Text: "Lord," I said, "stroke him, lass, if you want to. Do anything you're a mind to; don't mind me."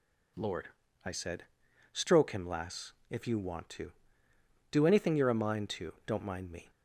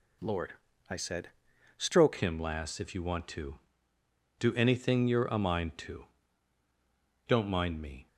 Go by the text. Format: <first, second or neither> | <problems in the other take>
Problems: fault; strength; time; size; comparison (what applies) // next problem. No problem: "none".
first | changes voice at "him"; from 2.1 s on; 5.9 s long